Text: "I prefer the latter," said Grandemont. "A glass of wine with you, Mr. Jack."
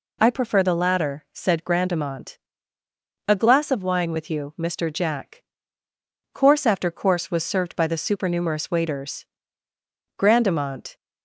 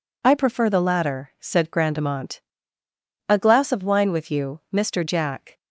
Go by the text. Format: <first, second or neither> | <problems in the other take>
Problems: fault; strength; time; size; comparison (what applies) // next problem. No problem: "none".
second | goes on to say "Course after course was served by the supernumerous waiters Grandemont"; strong; from 6.3 s on; 4.6 s long